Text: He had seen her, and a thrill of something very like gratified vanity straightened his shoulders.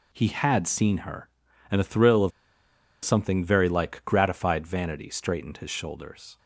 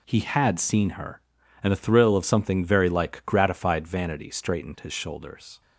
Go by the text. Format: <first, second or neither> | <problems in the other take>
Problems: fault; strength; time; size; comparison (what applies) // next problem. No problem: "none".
second | pauses between "of" and "something"; noticeable; at 2.3 s; 0.74 s long